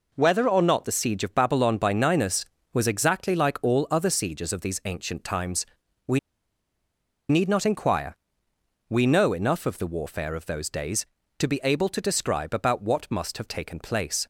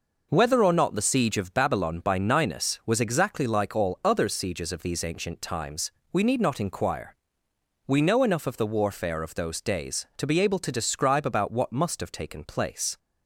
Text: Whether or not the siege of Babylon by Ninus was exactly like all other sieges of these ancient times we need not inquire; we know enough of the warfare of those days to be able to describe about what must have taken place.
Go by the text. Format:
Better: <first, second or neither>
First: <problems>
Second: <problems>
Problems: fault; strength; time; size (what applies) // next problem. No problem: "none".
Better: second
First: pauses between "times" and "we"; at 5.6 s; 0.42 s long // pauses between "we" and "need"; at 6.1 s; 1.1 s long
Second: pauses between "times" and "we"; slight; at 5.8 s; 0.22 s long